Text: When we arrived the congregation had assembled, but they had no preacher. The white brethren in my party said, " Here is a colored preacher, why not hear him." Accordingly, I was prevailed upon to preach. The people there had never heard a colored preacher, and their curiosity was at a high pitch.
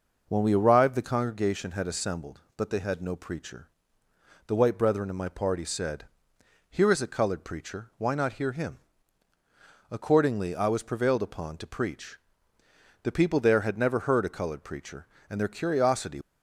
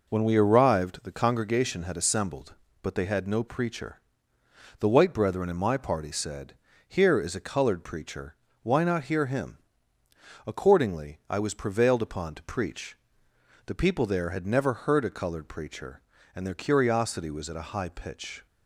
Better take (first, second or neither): second